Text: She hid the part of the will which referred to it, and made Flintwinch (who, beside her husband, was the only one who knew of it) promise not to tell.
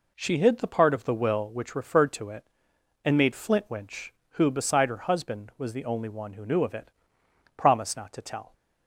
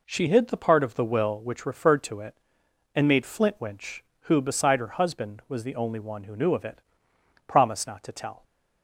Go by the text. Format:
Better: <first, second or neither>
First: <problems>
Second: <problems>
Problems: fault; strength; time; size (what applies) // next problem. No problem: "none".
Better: neither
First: none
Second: none